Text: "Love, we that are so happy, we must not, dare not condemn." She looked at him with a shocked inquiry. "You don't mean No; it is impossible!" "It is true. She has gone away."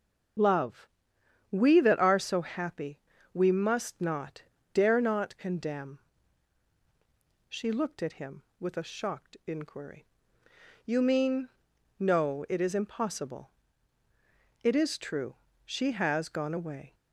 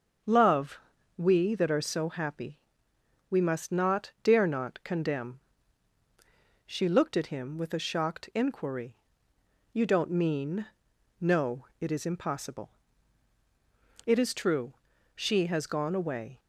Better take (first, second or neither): second